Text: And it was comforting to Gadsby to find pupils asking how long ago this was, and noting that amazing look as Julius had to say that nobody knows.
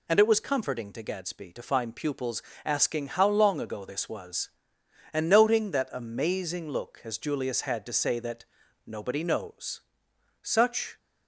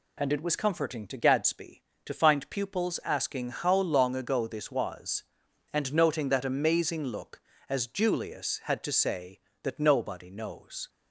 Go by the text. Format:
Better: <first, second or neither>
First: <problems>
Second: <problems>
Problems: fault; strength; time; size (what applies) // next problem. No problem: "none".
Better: second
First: pauses between "pupils" and "asking"; slight; at 2.4 s; 0.22 s long // pauses between "that" and "nobody"; at 8.4 s; 0.40 s long // goes on to say "Such"; from 10.4 s on; 0.54 s long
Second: none